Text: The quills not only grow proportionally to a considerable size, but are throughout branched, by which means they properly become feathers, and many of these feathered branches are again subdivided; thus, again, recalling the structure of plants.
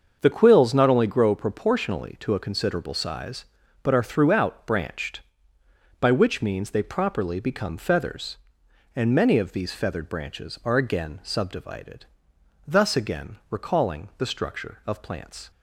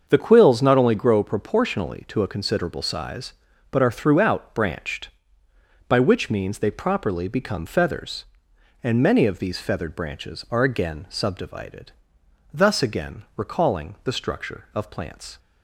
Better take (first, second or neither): neither